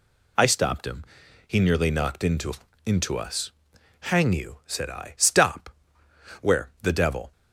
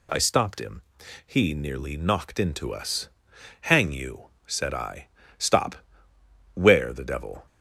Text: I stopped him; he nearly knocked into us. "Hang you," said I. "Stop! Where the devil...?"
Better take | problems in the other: second | says "into" twice; at 2.8 s

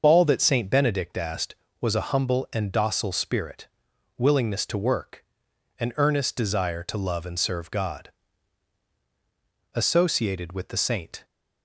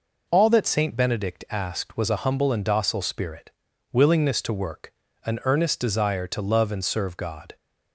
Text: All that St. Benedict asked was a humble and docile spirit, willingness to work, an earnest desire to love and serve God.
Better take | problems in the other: second | starts louder than the rest; until 1.0 s; 6.5 dB // goes on to say "Associated with the Saint"; from 9.7 s on; 1.5 s long

